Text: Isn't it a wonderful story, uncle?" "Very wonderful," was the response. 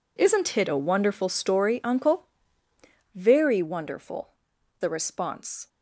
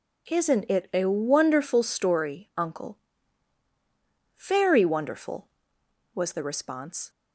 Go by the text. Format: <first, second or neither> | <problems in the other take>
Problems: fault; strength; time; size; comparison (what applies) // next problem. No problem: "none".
second | skips "was"; at 4.5 s